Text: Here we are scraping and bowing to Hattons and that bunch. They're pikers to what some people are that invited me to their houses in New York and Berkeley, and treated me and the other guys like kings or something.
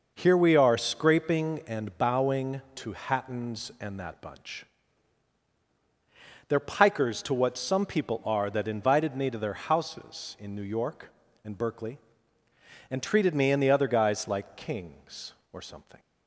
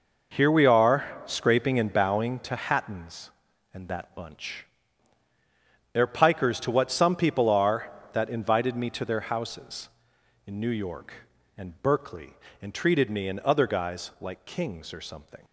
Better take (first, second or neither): first